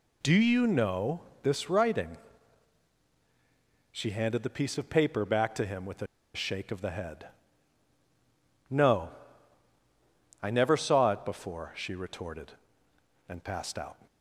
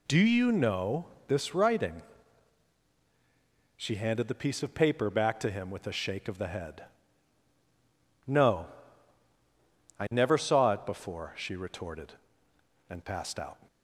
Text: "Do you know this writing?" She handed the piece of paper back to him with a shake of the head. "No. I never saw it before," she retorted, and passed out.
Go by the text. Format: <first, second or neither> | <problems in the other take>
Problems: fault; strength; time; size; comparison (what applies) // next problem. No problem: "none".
second | pauses between "know" and "this"; slight; at 1.2 s; 0.20 s long; slight in the second // pauses between "a" and "shake"; slight; at 6.0 s; 0.29 s long